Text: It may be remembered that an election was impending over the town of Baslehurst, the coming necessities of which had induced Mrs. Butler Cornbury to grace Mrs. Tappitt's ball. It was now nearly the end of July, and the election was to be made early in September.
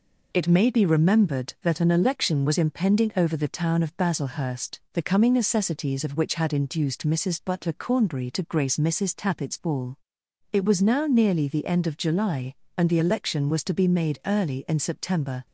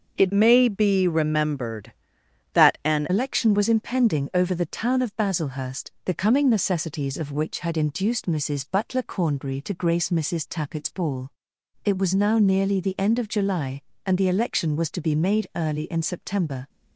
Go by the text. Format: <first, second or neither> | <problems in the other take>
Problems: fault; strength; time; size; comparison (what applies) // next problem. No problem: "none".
first | starts louder than the rest; until 1.1 s; 6.5 dB // changes voice from "may" to "an"; from 0.3 to 3.0 s; 2.7 s long